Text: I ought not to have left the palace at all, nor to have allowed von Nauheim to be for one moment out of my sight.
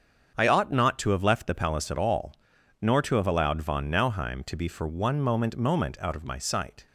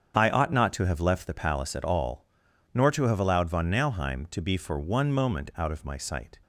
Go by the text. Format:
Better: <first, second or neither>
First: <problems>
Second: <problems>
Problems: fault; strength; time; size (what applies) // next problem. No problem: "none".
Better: second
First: starts louder than the rest; strong; until 1.3 s; 7.5 dB // says "moment" twice; at 5.5 s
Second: starts louder than the rest; strong; until 1.2 s; 7.5 dB